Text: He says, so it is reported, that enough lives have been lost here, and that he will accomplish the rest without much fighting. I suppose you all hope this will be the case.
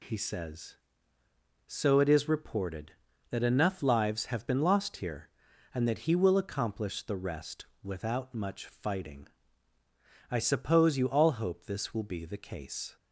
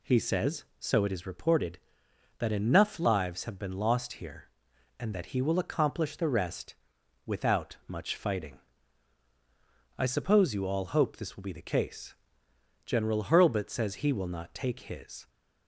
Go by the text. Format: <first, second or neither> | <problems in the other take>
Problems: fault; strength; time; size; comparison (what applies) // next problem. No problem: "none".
first | pauses between "rest" and "without"; noticeable; at 6.7 s; 0.52 s long; slight in the first // goes on to say "General Hurlbut says he will not take his"; strong; from 12.8 s on; 2.4 s long